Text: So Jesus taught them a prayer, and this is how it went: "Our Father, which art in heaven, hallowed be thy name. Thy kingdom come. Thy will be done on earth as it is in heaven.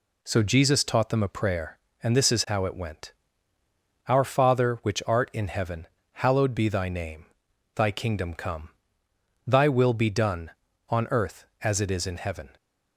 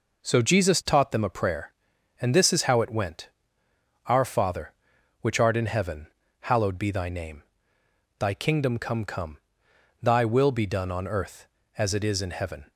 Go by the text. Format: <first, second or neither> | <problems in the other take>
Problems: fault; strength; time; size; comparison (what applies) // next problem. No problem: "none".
first | says "come" twice; at 9.0 s